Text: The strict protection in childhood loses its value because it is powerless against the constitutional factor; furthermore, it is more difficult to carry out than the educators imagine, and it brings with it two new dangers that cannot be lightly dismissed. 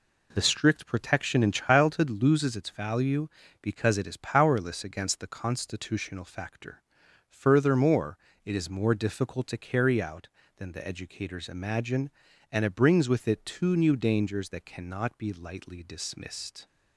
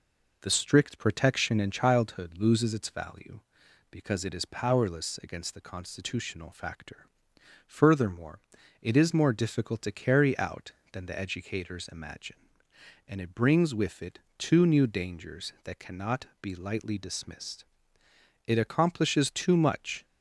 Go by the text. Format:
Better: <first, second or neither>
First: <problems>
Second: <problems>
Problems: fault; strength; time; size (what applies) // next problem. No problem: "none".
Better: first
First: none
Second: pauses between "it" and "two"; slight; at 14.2 s; 0.16 s long // goes on to say "It accomplishes too much"; from 18.4 s on; 1.5 s long